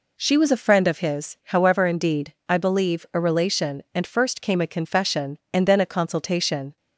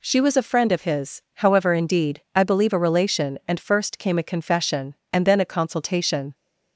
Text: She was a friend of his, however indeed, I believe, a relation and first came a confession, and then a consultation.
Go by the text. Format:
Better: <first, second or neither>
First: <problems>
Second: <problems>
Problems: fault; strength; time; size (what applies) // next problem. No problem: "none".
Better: neither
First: none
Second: none